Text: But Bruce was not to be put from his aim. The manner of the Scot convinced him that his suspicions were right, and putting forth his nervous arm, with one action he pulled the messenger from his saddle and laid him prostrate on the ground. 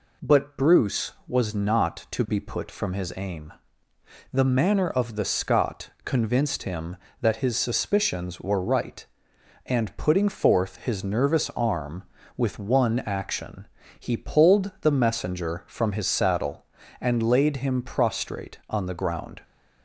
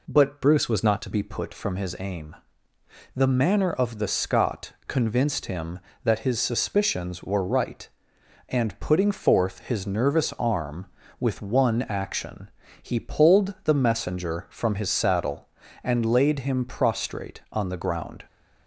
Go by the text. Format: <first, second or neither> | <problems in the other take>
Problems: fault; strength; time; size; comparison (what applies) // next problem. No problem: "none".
first | changes voice from "Bruce" to "to"; from 0.4 to 1.0 s; 0.6 s long // pauses between "action" and "he"; slight; at 12.4 s; 0.32 s long; slight in the first